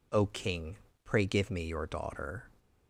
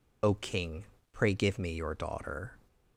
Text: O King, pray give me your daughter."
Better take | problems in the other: first | loses the start of "O"; at 0.2 s; 35 ms

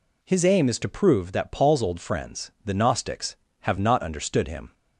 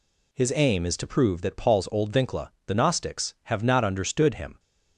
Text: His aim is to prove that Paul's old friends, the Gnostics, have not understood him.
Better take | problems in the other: first | says "vincla" for "friends"; at 2.1 s

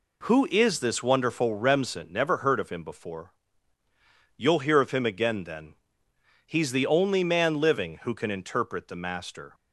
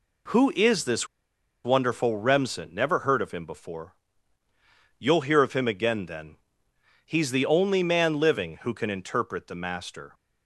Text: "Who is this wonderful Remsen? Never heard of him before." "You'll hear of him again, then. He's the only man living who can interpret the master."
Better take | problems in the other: first | pauses between "this" and "wonderful"; noticeable; at 1.0 s; 0.57 s long

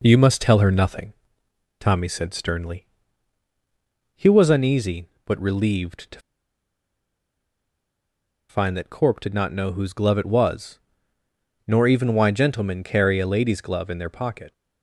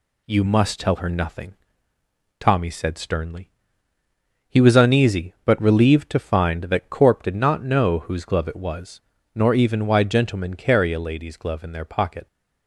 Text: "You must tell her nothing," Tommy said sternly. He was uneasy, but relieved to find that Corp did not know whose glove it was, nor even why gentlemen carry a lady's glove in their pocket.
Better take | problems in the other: second | pauses between "to" and "find"; strong; at 6.1 s; 2.3 s long

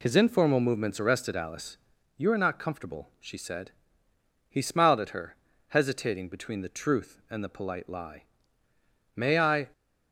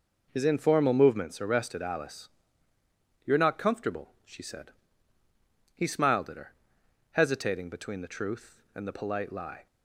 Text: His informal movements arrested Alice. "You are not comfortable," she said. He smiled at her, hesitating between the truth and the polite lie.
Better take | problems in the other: second | goes on to say "May I"; from 9.1 s on; 0.54 s long

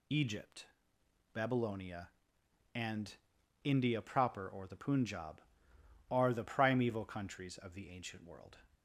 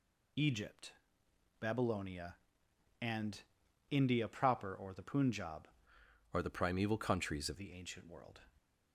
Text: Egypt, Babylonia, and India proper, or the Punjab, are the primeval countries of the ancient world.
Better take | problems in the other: first | pauses between "and" and "India"; noticeable; at 3.3 s; 0.52 s long; noticeable in the first // changes voice from "are" to "of"; from 6.3 to 7.5 s; 1.2 s long

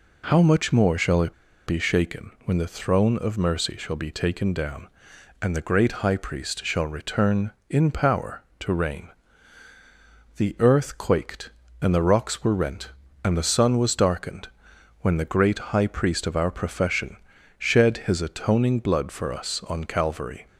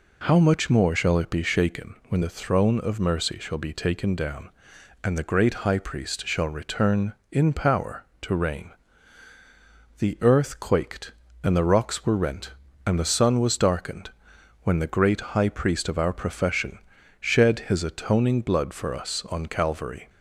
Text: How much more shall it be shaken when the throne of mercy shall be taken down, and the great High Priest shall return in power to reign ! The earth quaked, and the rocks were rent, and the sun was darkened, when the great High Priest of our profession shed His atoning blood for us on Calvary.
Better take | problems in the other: second | pauses between "it" and "be"; slight; at 1.3 s; 0.33 s long // pauses between "profession" and "shed"; at 17.1 s; 0.42 s long; also in the second

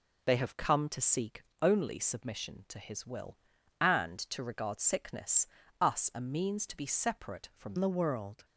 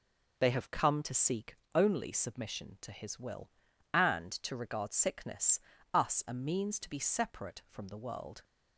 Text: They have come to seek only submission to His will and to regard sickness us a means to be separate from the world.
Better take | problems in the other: second | pauses between "seek" and "only"; slight; at 1.4 s; 0.18 s long; slight in the second // pauses between "sickness" and "us"; slight; at 5.4 s; 0.34 s long; slight in the second // changes voice at "the"; from 7.7 s on; 0.7 s long

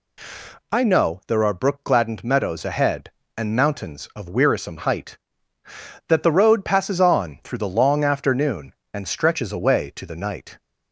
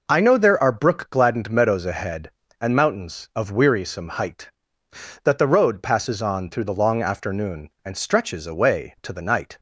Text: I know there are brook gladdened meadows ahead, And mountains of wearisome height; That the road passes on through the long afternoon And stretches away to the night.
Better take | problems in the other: neither | none

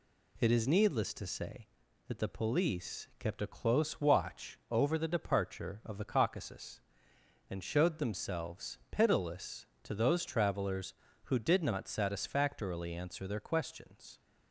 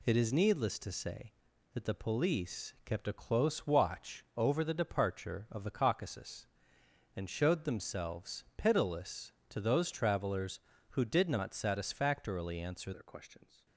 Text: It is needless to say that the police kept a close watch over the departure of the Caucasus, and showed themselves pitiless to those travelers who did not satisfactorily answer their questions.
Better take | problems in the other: first | changes voice at "their"; from 12.9 s on; 0.7 s long

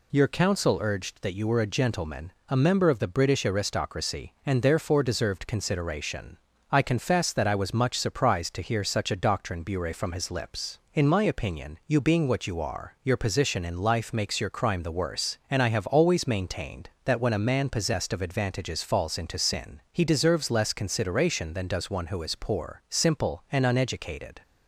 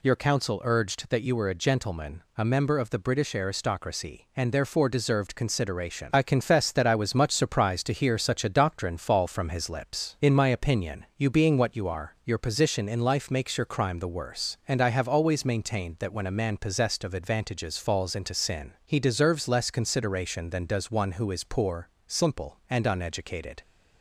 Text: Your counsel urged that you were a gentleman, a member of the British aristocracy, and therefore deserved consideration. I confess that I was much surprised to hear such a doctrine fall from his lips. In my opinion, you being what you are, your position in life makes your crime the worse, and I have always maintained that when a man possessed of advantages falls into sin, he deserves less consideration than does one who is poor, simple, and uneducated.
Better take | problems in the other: second | says "bure" for "fall"; at 9.6 s

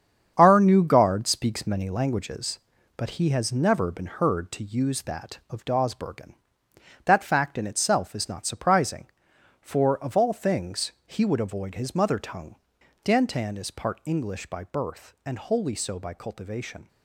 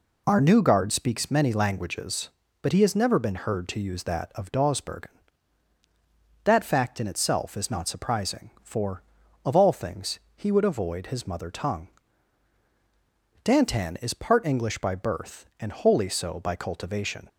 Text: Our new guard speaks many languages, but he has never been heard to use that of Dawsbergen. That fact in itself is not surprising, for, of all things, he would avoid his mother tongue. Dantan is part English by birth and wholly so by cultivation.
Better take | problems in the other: second | gets quieter; strong; throughout; 8.5 dB

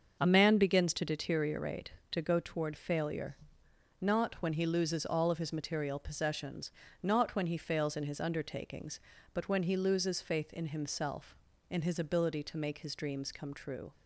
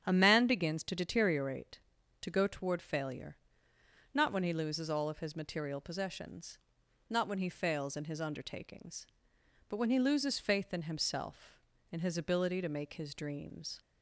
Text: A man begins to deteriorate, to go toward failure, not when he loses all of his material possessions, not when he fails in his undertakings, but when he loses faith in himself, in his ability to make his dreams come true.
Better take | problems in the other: first | starts louder than the rest; strong; until 1.0 s; 9 dB; also in the first // stops before "come true"; at 13.7 s

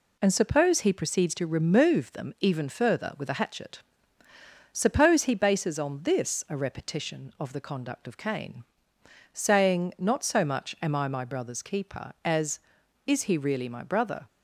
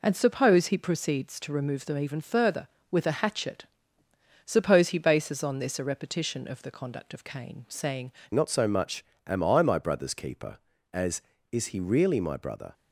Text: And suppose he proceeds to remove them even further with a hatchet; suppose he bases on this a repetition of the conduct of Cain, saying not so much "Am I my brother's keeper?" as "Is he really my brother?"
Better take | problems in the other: first | changes voice at "not"; from 8.3 s on; 4.4 s long // pauses between "much" and "Am"; slight; at 9.0 s; 0.22 s long

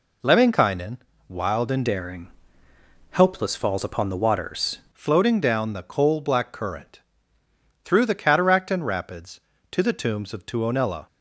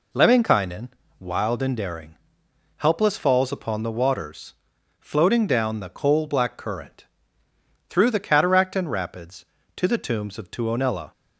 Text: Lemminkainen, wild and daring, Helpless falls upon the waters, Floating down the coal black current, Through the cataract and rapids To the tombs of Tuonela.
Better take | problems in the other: second | changes voice from "daring" to "waters"; from 1.8 to 4.7 s; 2.9 s long

